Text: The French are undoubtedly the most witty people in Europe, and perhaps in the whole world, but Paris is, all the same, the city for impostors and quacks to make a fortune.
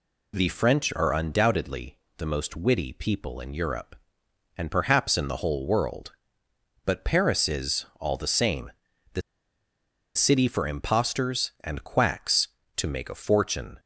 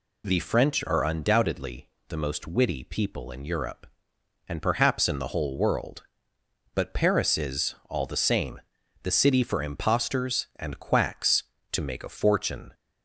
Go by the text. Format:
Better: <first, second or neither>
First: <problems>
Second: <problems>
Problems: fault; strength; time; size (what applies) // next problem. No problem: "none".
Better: second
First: pauses between "undoubtedly" and "the"; slight; at 1.9 s; 0.22 s long // pauses between "the" and "city"; noticeable; at 9.2 s; 0.94 s long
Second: pauses between "undoubtedly" and "the"; slight; at 1.8 s; 0.22 s long